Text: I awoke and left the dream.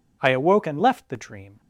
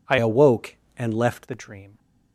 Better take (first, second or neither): first